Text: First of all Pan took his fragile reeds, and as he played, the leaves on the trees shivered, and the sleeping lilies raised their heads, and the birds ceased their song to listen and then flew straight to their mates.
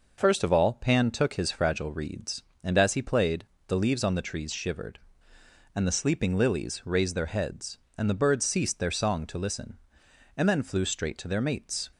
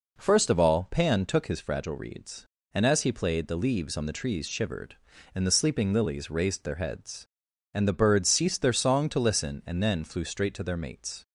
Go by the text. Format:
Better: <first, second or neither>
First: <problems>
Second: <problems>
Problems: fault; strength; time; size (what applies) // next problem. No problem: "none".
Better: neither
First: none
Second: none